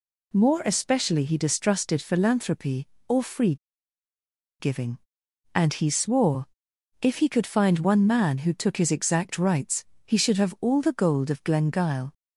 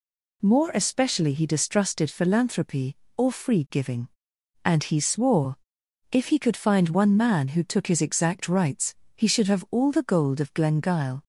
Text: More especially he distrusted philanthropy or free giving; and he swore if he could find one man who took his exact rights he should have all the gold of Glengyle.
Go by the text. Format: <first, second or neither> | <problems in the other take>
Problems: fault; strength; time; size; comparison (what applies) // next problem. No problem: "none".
second | pauses between "free" and "giving"; at 3.5 s; 1.0 s long // pauses between "swore" and "if"; noticeable; at 6.4 s; 0.54 s long; noticeable in the second // pauses between "rights" and "he"; slight; at 9.8 s; 0.20 s long; slight in the second